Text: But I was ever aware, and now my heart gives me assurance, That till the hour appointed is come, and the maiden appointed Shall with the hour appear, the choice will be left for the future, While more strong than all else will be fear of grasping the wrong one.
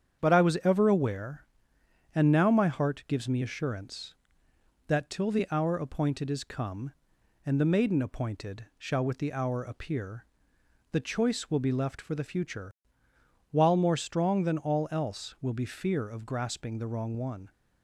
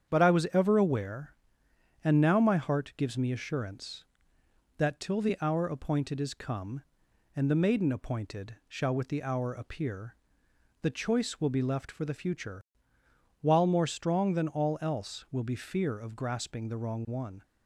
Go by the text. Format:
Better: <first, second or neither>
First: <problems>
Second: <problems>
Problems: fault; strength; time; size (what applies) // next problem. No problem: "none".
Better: neither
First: starts louder than the rest; strong; until 1.2 s; 8 dB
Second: starts louder than the rest; strong; until 1.1 s; 8 dB